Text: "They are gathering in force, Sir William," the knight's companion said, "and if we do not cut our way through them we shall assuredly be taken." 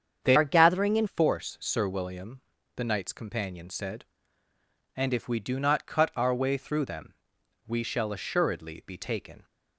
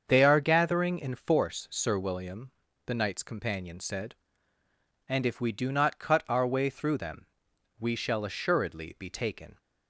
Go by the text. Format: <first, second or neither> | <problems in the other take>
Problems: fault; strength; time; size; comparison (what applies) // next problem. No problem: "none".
second | starts louder than the rest; strong; until 1.2 s; 7.5 dB; also in the second // changes voice from "are" to "in"; from 0.3 to 1.0 s; 0.7 s long // pauses between "them" and "we"; noticeable; at 7.1 s; 0.54 s long; noticeable in the second